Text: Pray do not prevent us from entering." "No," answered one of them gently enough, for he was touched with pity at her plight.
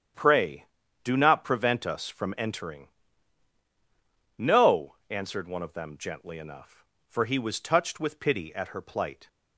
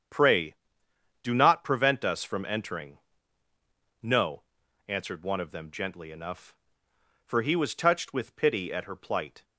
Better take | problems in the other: neither | starts louder than the rest; strong; the same in both

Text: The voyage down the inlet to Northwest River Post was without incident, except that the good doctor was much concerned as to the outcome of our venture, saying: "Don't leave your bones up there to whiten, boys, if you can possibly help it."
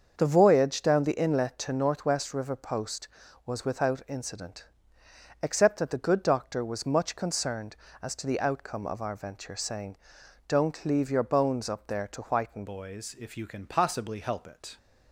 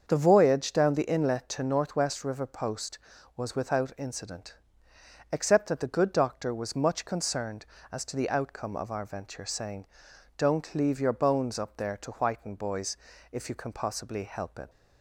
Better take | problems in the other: second | starts louder than the rest; until 1.1 s; 6.5 dB; also in the second // changes voice at "boys"; from 12.6 s on; 2.1 s long

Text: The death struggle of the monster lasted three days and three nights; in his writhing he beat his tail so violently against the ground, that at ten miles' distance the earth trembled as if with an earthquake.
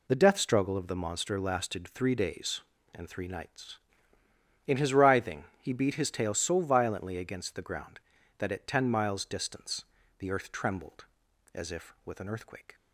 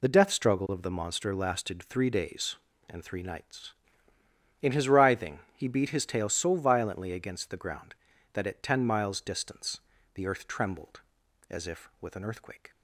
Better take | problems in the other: neither | pauses between "writhing" and "he"; slight; the same in both // pauses between "distance" and "the"; slight; the same in both

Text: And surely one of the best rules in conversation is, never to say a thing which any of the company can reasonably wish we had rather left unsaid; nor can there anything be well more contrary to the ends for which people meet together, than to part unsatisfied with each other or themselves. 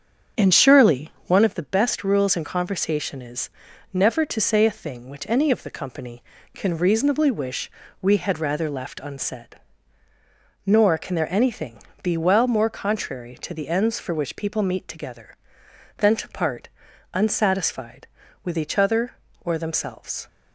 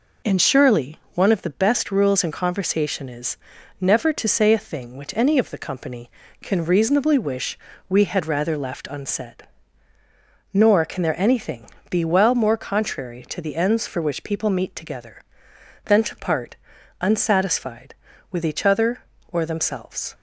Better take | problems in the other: second | starts louder than the rest; strong; until 1.5 s; 7.5 dB // pauses between "surely" and "one"; slight; at 1.1 s; 0.16 s long; slight in the second // pauses between "wish" and "we"; slight; at 7.7 s; 0.30 s long; slight in the second // pauses between "anything" and "be"; slight; at 11.8 s; 0.22 s long; slight in the second // pauses between "part" and "unsatisfied"; noticeable; at 16.6 s; 0.46 s long; noticeable in the second

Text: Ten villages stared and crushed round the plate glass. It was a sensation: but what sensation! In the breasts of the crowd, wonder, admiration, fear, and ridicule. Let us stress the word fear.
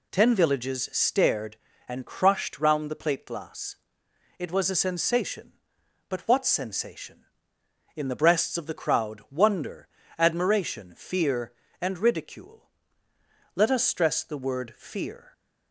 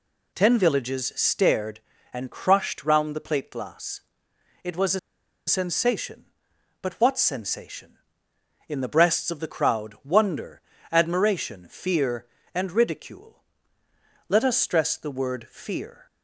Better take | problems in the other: first | pauses between "a" and "sensation"; noticeable; at 4.9 s; 0.48 s long

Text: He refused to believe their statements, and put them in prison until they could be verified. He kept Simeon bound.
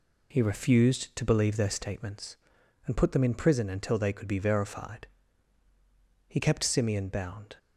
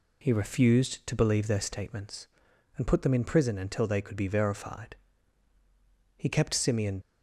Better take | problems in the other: first | stops before "bound"; at 7.0 s

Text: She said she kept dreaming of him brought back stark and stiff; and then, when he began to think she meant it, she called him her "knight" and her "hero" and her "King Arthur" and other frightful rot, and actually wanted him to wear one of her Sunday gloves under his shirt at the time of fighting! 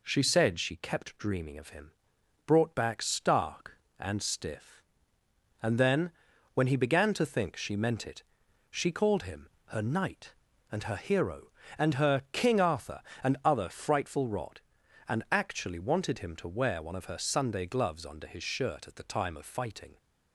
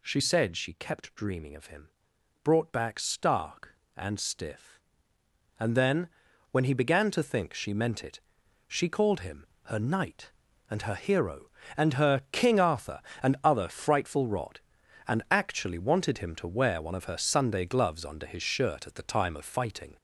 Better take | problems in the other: first | gets louder; noticeable; throughout; 4.5 dB // pauses between "him" and "brought"; noticeable; at 1.8 s; 0.54 s long; noticeable in the first // pauses between "him" and "her"; slight; at 9.4 s; 0.20 s long; slight in the first

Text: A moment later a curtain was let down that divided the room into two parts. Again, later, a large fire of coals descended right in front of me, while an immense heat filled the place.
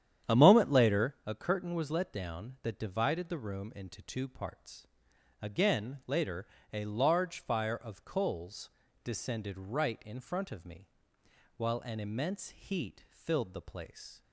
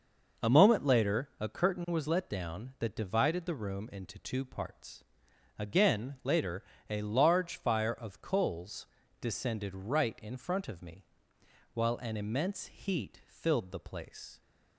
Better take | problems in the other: second | starts louder than the rest; strong; until 1.2 s; 9.5 dB // pauses between "coals" and "descended"; slight; at 8.6 s; 0.34 s long; slight in the second

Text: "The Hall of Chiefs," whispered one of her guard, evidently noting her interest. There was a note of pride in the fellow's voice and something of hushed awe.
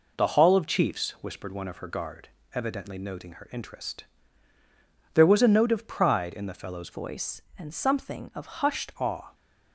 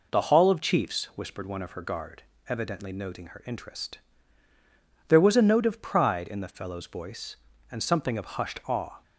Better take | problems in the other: second | changes voice from "voice" to "hushed"; from 6.9 to 8.9 s; 2.0 s long

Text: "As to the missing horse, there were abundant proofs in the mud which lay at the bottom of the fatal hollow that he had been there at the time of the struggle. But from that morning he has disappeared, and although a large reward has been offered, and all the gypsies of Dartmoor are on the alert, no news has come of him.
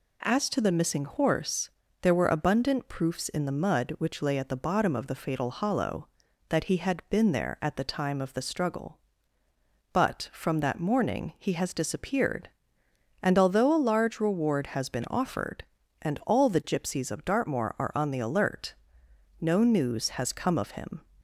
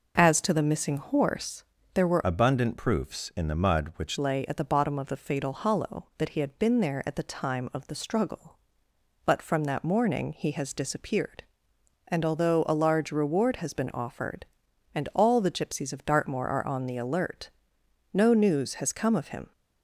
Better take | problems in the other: first | changes voice from "abundant" to "which"; from 2.2 to 4.1 s; 1.9 s long

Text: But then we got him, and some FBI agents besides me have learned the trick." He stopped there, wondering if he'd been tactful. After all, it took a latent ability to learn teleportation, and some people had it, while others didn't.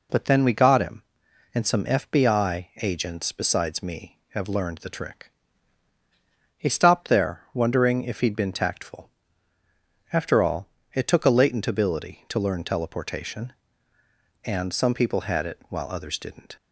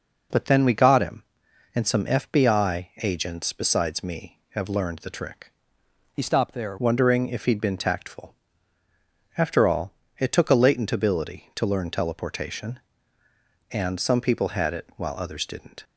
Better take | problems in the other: first | changes voice from "He" to "there"; from 6.1 to 6.7 s; 0.6 s long

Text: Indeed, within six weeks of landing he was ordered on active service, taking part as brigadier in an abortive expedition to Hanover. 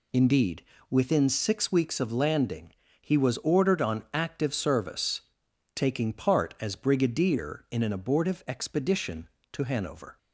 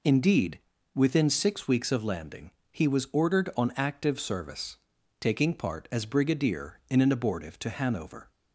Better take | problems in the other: first | pauses between "landing" and "he"; slight; at 2.5 s; 0.22 s long; slight in the first // skips "expedition"; at 7.5 s

